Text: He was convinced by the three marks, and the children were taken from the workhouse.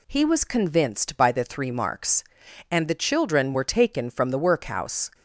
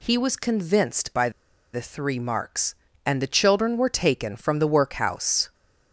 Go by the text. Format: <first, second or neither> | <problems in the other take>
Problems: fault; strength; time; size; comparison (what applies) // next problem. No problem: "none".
first | pauses between "by" and "the"; at 1.2 s; 0.43 s long